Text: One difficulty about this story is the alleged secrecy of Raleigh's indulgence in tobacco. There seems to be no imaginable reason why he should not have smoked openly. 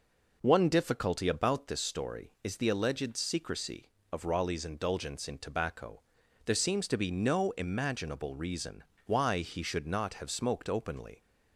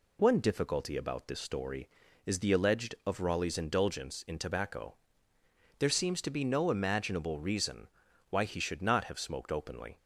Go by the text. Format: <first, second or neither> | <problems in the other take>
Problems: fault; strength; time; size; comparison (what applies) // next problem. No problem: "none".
first | skips "secrecy"; at 3.0 s // pauses between "reason" and "why"; at 7.8 s; 0.42 s long; slight in the first